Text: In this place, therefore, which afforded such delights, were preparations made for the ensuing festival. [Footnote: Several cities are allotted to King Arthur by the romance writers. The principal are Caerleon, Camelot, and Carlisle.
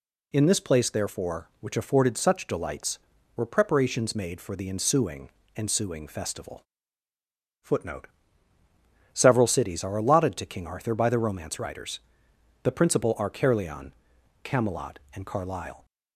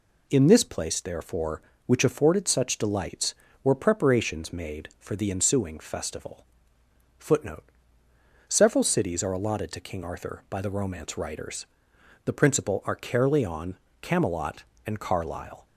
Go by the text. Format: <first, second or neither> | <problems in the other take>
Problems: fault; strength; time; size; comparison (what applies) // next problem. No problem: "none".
second | says "ensuing" twice; at 5.5 s